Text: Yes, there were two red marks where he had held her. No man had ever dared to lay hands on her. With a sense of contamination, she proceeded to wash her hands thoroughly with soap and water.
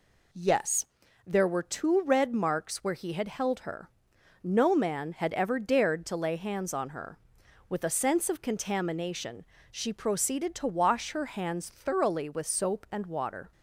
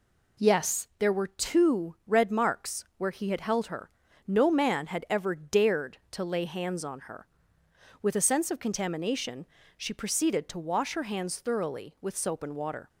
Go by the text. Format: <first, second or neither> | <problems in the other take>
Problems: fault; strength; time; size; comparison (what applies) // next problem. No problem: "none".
neither | none